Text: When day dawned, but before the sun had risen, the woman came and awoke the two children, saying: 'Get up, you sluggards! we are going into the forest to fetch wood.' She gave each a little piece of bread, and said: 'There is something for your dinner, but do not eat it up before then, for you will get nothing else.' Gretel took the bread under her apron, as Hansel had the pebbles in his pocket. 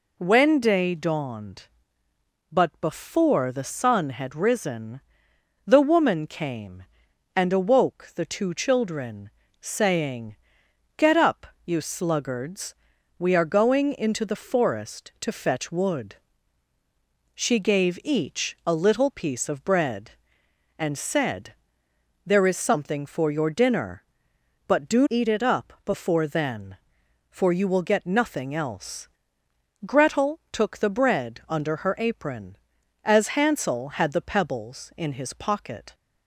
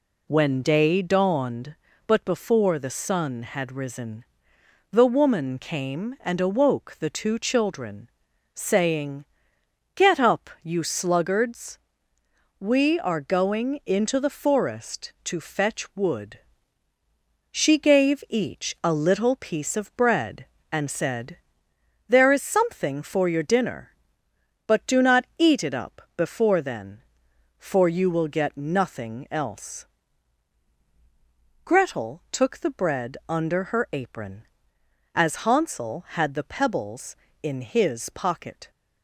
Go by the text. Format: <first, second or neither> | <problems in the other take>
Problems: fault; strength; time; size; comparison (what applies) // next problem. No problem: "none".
second | skips "not"; at 25.0 s